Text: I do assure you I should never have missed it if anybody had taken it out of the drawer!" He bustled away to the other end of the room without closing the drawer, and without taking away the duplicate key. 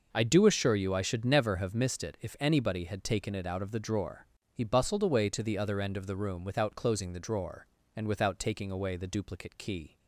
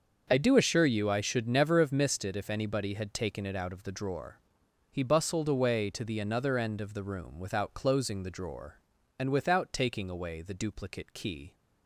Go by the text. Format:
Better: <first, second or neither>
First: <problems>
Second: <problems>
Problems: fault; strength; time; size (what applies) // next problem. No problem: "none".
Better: first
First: none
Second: starts louder than the rest; until 1.3 s; 6.5 dB // says "another" for "other"; at 6.1 s